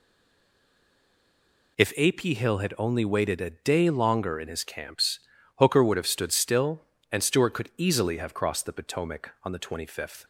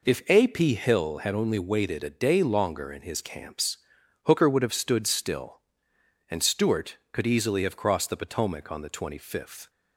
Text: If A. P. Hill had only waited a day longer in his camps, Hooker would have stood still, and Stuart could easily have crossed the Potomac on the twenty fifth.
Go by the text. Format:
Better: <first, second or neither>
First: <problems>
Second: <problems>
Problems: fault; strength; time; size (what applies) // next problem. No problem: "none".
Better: second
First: stays silent before the first word; noticeable; until 1.7 s; 1.7 s long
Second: none